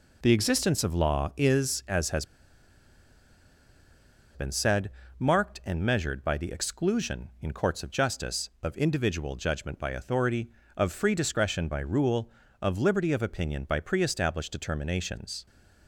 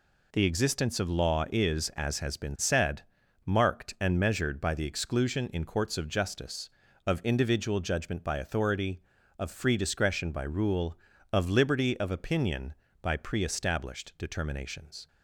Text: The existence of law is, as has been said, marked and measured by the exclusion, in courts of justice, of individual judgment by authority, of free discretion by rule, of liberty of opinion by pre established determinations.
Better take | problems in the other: second | pauses between "has" and "been"; strong; at 2.2 s; 2.1 s long

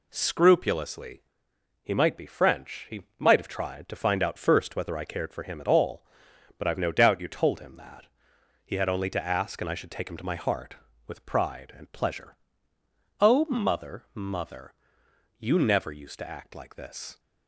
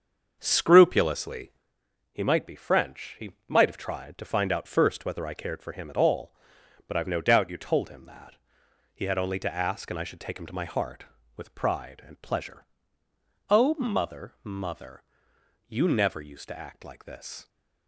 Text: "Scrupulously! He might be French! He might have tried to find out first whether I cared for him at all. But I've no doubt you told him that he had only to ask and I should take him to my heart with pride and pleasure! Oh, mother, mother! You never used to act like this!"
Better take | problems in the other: first | starts louder than the rest; until 1.7 s; 6.5 dB // pauses between "He" and "might"; slight; at 3.3 s; 0.16 s long; slight in the first // pauses between "that" and "he"; noticeable; at 8.3 s; 0.60 s long; noticeable in the first

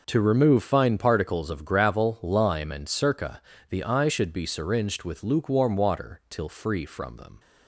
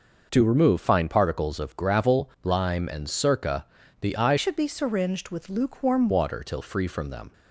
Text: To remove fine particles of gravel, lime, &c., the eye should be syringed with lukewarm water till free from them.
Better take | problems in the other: first | changes voice from "should" to "lukewarm"; from 4.3 to 6.0 s; 1.7 s long

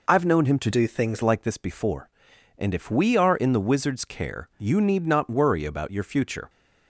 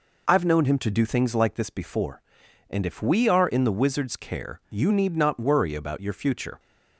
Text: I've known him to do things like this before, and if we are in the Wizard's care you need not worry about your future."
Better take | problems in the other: second | changes voice from "do" to "things"; from 0.7 to 1.2 s; 0.5 s long

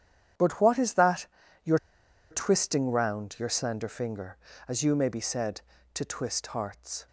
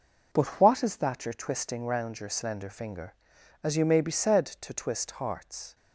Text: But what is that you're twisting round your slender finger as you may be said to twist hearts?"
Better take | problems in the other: second | starts louder than the rest; strong; until 1.7 s; 9.5 dB // pauses between "that" and "you're"; slight; at 1.2 s; 0.36 s long // pauses between "you're" and "twisting"; noticeable; at 1.7 s; 0.53 s long

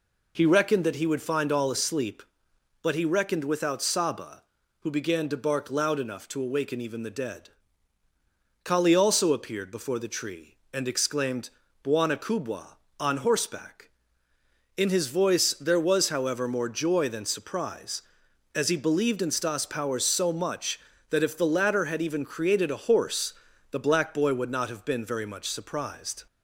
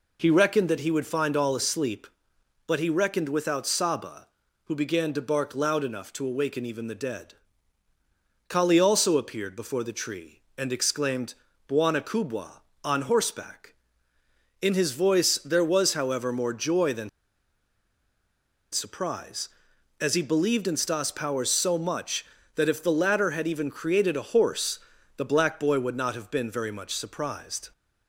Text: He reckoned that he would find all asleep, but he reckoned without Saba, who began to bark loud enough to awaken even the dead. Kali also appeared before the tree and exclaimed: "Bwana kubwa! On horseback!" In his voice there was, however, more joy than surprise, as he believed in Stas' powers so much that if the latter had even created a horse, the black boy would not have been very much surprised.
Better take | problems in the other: first | pauses between "than" and "surprise"; strong; at 17.0 s; 1.6 s long

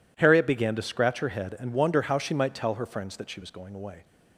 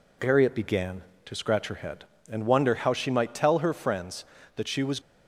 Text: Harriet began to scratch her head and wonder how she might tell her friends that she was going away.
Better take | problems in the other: first | stops before "going away"; at 4.9 s

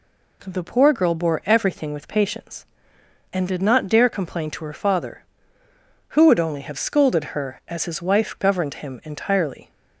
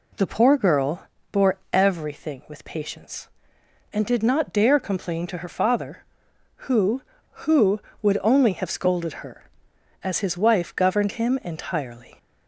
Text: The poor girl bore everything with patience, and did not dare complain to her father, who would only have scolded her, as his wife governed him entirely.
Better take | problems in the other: first | pauses between "girl" and "bore"; slight; at 1.0 s; 0.24 s long // says "who" twice; at 7.4 s

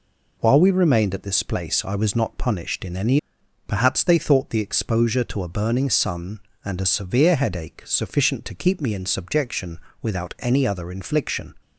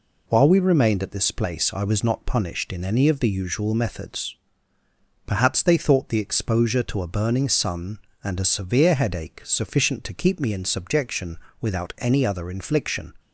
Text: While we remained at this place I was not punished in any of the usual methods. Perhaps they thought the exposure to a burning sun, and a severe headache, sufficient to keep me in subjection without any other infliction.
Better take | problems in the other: second | skips "of the usual methods"; at 3.4 s // pauses between "subjection" and "without"; slight; at 9.7 s; 0.24 s long; slight in the second

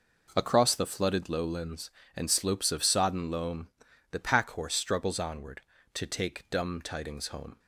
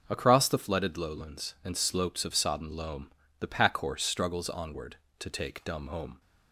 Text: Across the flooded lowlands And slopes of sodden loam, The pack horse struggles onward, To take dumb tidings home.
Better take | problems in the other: first | skips "tidings"; at 5.8 s

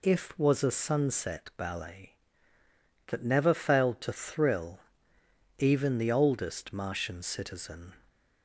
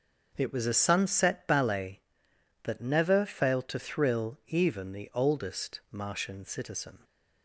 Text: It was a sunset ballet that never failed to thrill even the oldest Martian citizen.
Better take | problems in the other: second | says "If" for "It"; at 0.0 s // pauses between "thrill" and "even"; noticeable; at 4.7 s; 0.80 s long

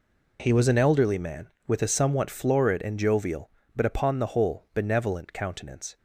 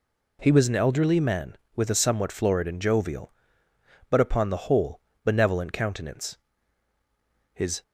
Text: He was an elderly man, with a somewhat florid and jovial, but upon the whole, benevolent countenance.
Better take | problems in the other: first | goes on to say "His"; slight; from 7.5 s on; 0.30 s long

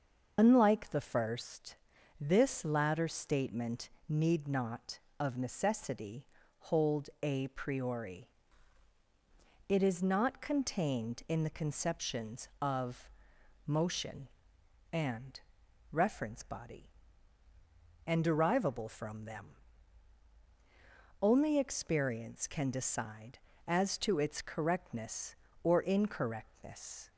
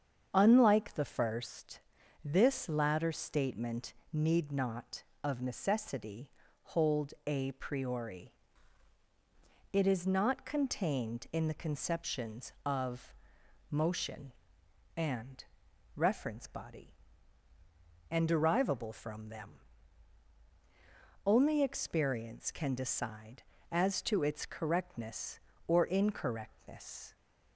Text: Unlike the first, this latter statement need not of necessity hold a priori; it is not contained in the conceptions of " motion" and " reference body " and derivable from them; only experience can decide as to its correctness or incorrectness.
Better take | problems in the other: second | loses the start of "Unlike"; at 0.3 s; 85 ms // starts louder than the rest; until 1.3 s; 6.5 dB; strong in the second // pauses between "statement" and "need"; slight; at 3.8 s; 0.20 s long; slight in the second // pauses between "necessity" and "hold"; slight; at 6.2 s; 0.32 s long; slight in the second

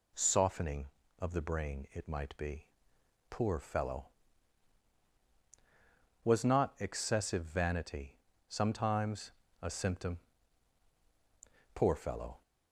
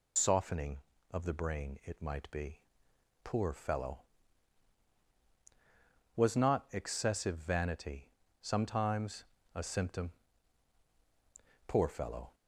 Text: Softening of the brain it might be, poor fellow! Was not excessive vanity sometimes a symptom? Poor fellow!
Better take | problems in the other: first | loses the start of "Softening"; at 0.1 s; 100 ms // pauses between "vanity" and "sometimes"; slight; at 8.1 s; 0.32 s long; slight in the first // pauses between "sometimes" and "a"; slight; at 9.2 s; 0.30 s long; slight in the first

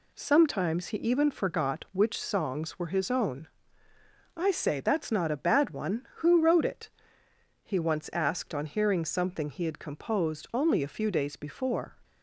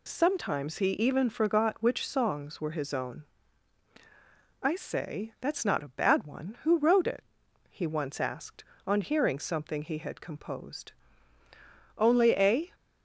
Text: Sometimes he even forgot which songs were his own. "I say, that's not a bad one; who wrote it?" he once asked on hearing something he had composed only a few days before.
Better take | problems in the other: first | pauses between "composed" and "only"; at 10.9 s; 1.0 s long // stops before "few days before"; at 12.7 s

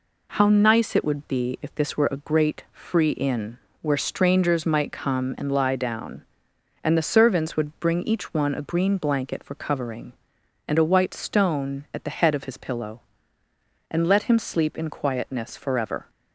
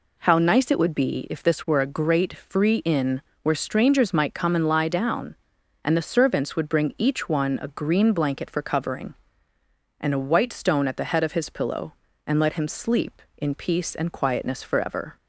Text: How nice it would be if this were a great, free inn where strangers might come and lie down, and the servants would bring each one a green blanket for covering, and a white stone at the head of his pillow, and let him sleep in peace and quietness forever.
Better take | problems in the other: second | pauses between "inn" and "where"; slight; at 3.5 s; 0.24 s long; slight in the second // skips "peace and"; at 14.9 s

